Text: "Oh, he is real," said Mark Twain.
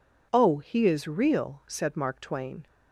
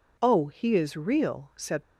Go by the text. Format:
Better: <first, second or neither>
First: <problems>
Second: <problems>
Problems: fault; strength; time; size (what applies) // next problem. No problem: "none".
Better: first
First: none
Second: stops before "Mark Twain"; at 1.8 s